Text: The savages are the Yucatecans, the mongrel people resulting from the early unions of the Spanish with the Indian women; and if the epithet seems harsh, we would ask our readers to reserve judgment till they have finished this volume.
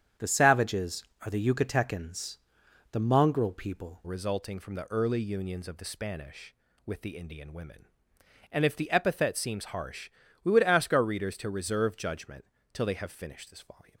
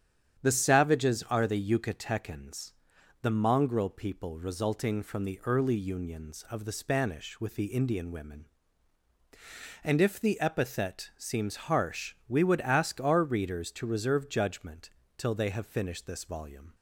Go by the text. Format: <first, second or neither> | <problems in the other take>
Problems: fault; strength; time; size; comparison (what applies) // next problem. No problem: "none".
second | starts louder than the rest; strong; until 1.4 s; 8.5 dB; strong in the second // changes voice at "resulting"; from 4.0 s on; 9.9 s long // pauses between "judgment" and "till"; slight; at 12.4 s; 0.28 s long; slight in the second